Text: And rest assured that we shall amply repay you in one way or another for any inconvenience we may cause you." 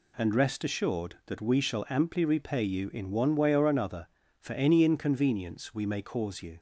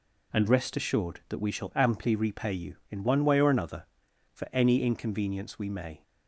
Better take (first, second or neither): first